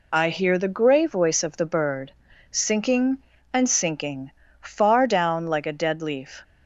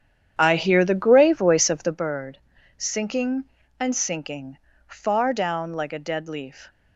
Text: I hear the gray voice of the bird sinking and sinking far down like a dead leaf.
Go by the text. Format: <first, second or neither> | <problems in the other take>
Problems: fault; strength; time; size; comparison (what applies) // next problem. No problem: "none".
first | starts louder than the rest; strong; until 2.0 s; 9 dB // pauses between "bird" and "sinking"; slight; at 2.3 s; 0.36 s long; slight in the first // pauses between "sinking" and "far"; slight; at 4.5 s; 0.30 s long; slight in the first